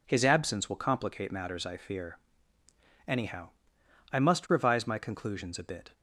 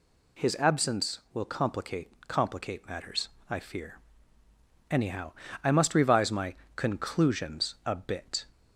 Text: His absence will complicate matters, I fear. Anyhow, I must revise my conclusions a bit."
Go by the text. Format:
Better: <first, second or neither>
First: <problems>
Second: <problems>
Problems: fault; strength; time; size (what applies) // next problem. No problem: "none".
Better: first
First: none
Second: says "complicate" twice; at 2.2 s // pauses between "my" and "conclusions"; slight; at 6.5 s; 0.24 s long